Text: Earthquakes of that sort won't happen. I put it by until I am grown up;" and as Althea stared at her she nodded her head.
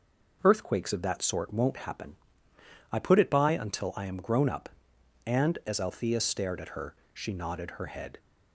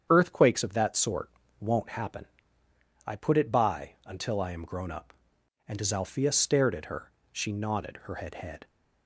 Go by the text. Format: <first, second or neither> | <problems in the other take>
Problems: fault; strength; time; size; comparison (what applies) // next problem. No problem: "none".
first | starts louder than the rest; strong; until 1.1 s; 8 dB // pauses between "sort" and "won't"; slight; at 1.2 s; 0.30 s long // pauses between "her" and "she"; slight; at 7.1 s; 0.22 s long; slight in the first // says "head" twice; at 8.3 s